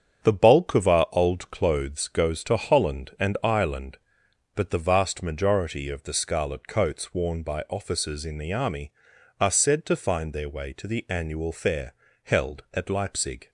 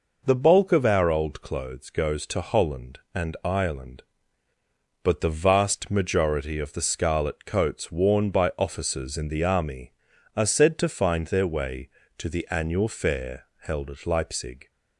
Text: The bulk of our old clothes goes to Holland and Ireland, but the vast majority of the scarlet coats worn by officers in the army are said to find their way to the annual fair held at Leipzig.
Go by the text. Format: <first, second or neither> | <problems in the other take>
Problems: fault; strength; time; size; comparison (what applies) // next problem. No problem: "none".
second | gets quieter; throughout; 7 dB // pauses between "fair" and "held"; slight; at 11.9 s; 0.28 s long